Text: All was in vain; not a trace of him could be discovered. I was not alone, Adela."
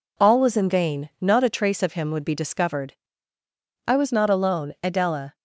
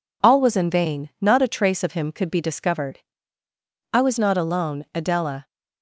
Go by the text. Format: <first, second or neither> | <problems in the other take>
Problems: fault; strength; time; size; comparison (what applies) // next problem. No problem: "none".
second | says "would" for "could"; at 2.1 s